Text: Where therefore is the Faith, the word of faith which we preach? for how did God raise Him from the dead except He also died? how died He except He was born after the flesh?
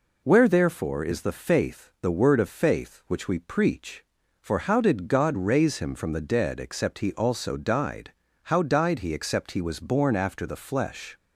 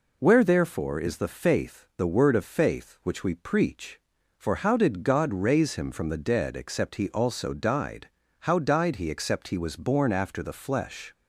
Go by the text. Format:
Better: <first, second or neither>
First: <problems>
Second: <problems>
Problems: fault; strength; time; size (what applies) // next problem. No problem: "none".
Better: neither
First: none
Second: none